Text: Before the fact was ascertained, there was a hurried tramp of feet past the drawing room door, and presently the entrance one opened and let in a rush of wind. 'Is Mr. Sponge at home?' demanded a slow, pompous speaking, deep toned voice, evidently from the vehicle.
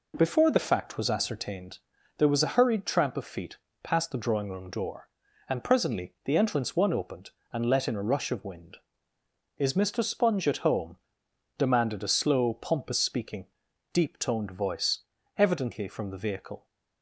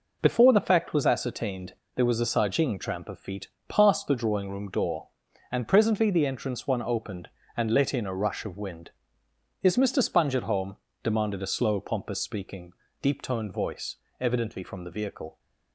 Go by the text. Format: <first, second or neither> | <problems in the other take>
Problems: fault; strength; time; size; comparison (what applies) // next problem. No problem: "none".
first | says "sajing" for "hurried"; at 2.2 s // pauses between "feet" and "past"; slight; at 3.4 s; 0.22 s long; slight in the first